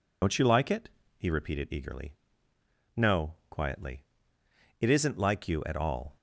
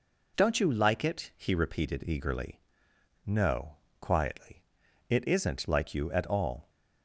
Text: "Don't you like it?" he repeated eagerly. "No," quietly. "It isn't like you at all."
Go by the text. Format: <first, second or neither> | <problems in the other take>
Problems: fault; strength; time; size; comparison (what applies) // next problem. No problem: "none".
second | loses the start of "Don't"; at 0.2 s; 75 ms